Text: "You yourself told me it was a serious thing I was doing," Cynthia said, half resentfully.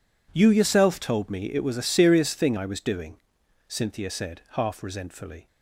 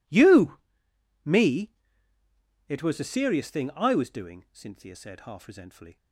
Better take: first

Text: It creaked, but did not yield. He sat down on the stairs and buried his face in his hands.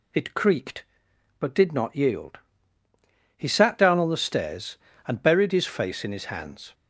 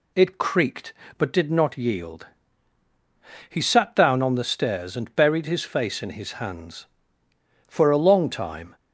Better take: first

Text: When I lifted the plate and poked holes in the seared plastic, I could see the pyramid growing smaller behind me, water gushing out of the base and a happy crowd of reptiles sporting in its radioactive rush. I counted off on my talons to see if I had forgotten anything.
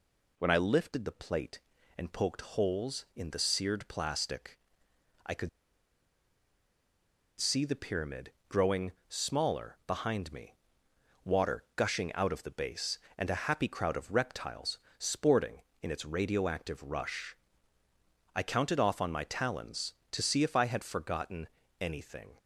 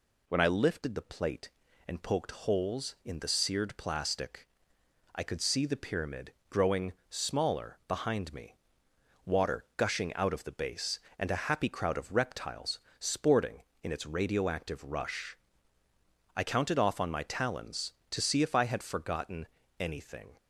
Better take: second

